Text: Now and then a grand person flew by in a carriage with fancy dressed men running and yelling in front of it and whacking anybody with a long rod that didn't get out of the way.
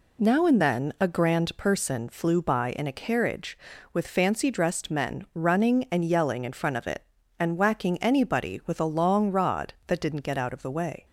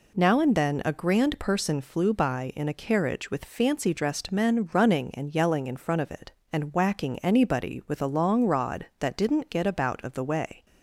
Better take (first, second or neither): first